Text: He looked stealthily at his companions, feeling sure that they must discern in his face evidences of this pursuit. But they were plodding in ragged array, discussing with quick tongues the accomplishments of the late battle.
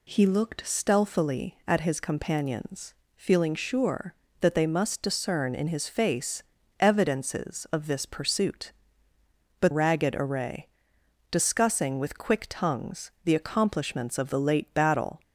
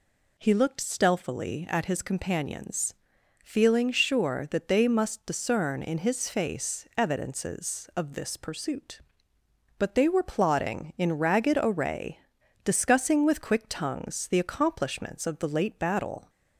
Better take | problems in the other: second | pauses between "face" and "evidences"; at 6.4 s; 0.38 s long // skips "they were plodding in"; at 9.7 s

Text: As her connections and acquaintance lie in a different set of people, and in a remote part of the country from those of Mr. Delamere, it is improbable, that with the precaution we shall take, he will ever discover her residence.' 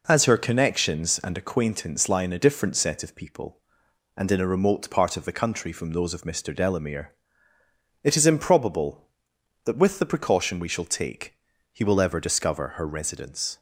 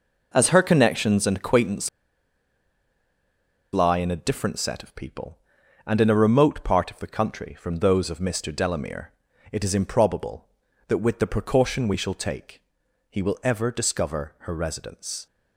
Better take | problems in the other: first | pauses between "acquaintance" and "lie"; strong; at 1.8 s; 1.8 s long

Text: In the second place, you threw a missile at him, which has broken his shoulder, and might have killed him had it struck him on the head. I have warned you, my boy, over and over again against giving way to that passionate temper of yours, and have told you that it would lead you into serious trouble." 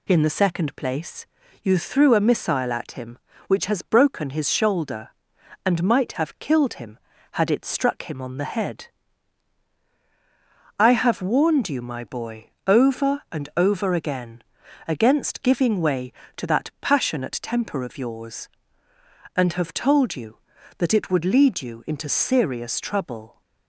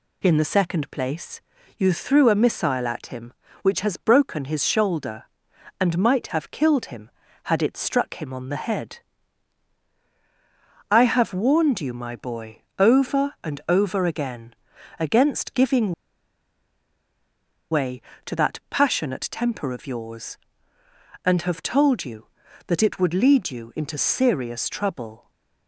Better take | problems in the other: first | pauses between "again" and "against"; at 14.5 s; 0.44 s long; also in the first // pauses between "giving" and "way"; strong; at 15.9 s; 1.7 s long

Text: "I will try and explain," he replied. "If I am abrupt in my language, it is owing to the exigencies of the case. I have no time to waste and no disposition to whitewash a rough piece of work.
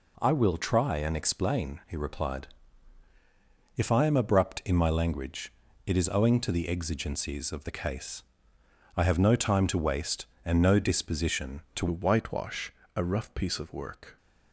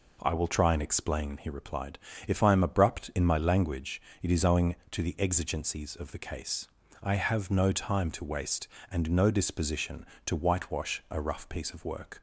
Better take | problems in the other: second | changes voice at "whitewash"; from 11.9 s on; 2.2 s long // pauses between "whitewash" and "a"; slight; at 12.7 s; 0.24 s long

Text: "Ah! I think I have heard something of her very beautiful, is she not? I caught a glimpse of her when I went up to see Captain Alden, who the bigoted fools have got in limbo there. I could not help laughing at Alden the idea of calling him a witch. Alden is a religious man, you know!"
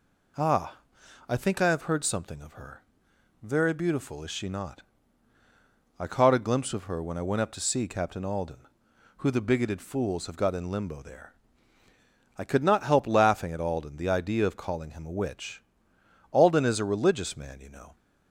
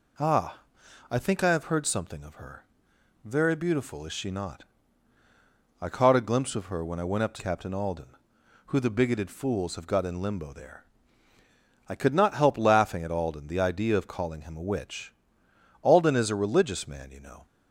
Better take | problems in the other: first | pauses between "her" and "very"; noticeable; at 2.6 s; 0.60 s long; noticeable in the first // skips "see"; at 7.3 s

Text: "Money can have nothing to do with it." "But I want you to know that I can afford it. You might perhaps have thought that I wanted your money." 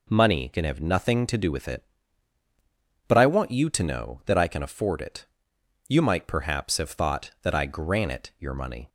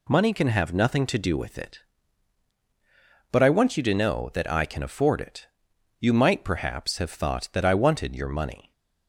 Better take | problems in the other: second | says "granite" for "wanted"; at 7.6 s

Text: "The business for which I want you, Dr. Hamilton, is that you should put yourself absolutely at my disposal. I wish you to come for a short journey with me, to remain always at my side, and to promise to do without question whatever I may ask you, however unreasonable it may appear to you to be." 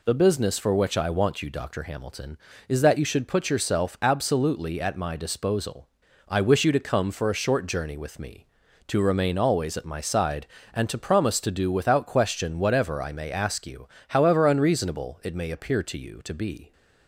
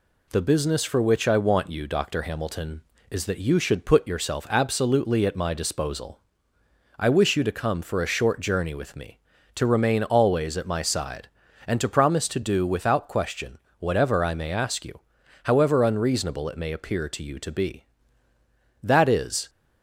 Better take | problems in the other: first | pauses between "question" and "whatever"; slight; at 13.5 s; 0.20 s long // goes on to say "That is"; noticeable; from 18.8 s on; 0.68 s long

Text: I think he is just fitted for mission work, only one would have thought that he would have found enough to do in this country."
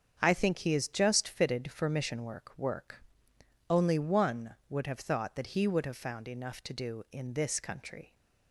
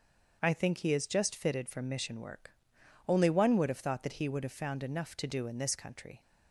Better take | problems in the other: second | starts louder than the rest; strong; until 1.2 s; 7.5 dB; also in the second // says "work" twice; at 2.5 s

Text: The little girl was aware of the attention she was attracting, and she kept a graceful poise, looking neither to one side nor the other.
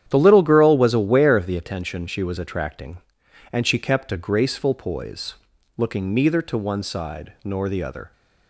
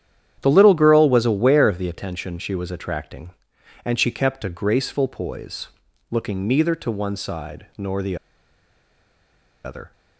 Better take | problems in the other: first | starts louder than the rest; strong; until 1.4 s; 9.5 dB; strong in the first // pauses between "the" and "other"; strong; at 8.1 s; 1.4 s long

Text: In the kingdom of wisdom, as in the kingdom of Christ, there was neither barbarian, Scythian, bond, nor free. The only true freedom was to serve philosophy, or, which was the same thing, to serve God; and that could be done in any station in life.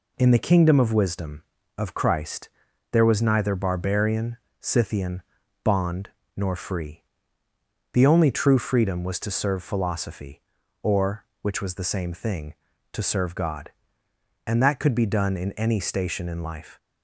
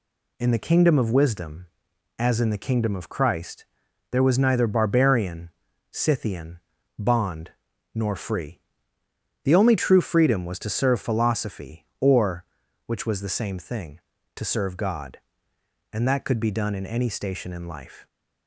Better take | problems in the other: second | skips "as in the kingdom"; at 1.5 s

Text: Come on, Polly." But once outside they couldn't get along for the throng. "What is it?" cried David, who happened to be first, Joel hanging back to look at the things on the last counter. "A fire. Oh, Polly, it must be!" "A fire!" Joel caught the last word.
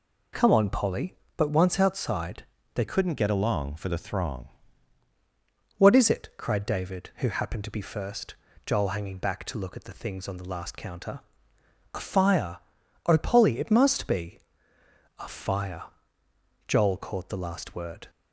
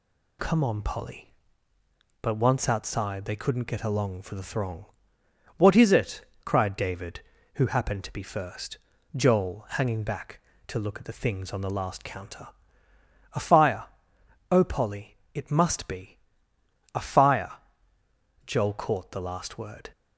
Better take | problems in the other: second | pauses between "outside" and "they"; slight; at 2.4 s; 0.30 s long // changes voice from "couldn't" to "throng"; from 2.8 to 4.4 s; 1.6 s long

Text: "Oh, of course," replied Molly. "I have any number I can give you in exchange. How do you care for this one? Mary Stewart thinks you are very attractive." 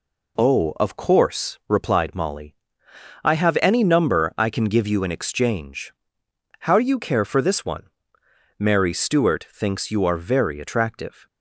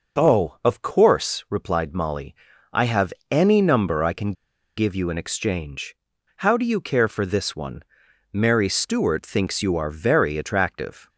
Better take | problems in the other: first | pauses between "have" and "any"; slight; at 3.1 s; 0.18 s long // pauses between "can" and "give"; at 4.3 s; 0.44 s long

